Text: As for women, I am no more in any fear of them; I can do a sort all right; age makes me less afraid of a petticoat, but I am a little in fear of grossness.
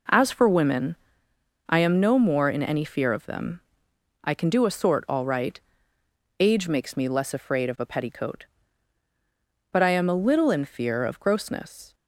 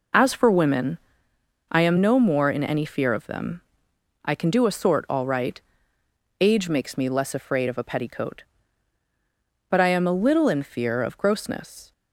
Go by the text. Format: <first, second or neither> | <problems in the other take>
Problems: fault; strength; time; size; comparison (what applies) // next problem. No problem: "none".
first | loses the start of "As"; at 0.1 s; 40 ms